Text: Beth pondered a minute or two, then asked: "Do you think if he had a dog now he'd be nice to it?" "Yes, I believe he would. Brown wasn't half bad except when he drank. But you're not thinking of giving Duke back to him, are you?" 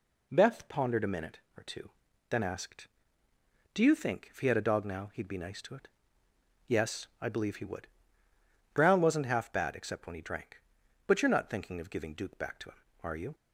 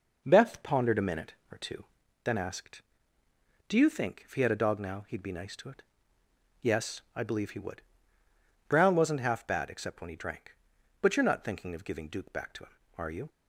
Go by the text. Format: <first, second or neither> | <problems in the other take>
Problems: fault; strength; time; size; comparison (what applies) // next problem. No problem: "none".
first | starts louder than the rest; noticeable; until 2.1 s; 5.5 dB